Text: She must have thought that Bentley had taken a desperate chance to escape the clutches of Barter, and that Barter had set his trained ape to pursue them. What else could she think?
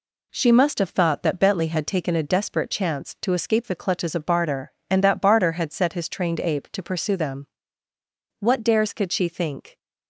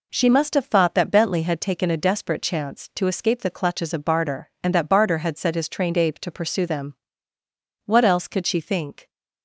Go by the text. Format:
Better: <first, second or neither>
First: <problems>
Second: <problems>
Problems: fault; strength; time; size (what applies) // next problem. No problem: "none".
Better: second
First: says "dares" for "else"; at 8.6 s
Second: none